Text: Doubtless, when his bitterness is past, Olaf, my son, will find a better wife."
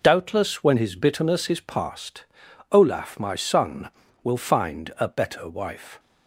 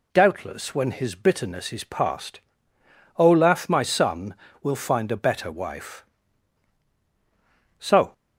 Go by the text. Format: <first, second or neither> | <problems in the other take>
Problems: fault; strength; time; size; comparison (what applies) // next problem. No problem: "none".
first | goes on to say "So"; slight; from 7.7 s on; 0.34 s long